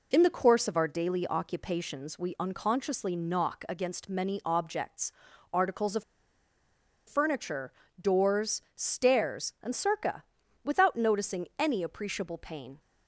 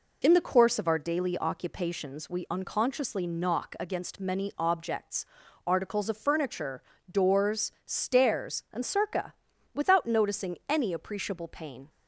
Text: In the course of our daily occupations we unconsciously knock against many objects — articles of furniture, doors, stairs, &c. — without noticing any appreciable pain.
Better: second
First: pauses between "of" and "furniture"; at 6.0 s; 1.0 s long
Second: none

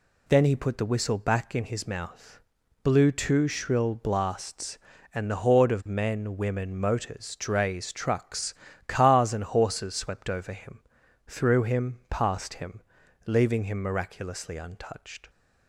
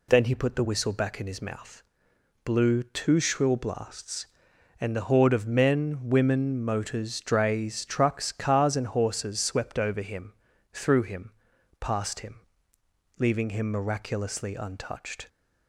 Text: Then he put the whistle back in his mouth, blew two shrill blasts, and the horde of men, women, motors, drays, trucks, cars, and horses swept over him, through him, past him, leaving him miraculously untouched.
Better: neither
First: none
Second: none

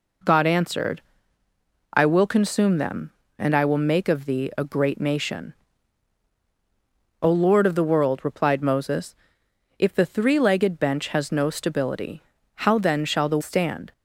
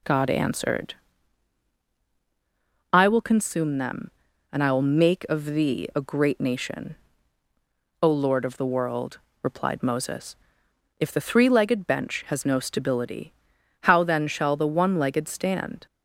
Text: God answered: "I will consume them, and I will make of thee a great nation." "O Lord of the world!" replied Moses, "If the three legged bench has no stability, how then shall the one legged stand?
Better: second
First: skips "one legged"; at 13.4 s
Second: none

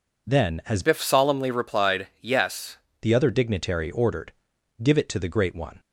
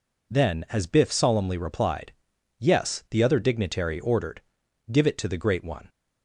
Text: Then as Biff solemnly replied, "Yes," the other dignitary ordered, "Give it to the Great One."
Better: second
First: changes voice from "Biff" to "Yes"; from 0.8 to 2.7 s; 1.9 s long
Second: none

